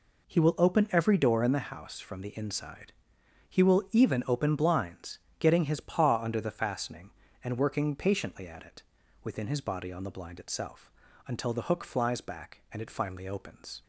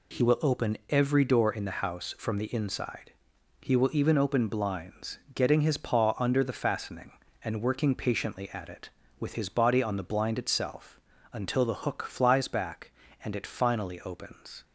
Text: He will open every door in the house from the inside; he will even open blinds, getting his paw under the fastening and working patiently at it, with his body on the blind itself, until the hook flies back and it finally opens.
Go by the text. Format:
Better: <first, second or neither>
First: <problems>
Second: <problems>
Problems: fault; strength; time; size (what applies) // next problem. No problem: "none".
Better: second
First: says "within" for "with"; at 9.2 s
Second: none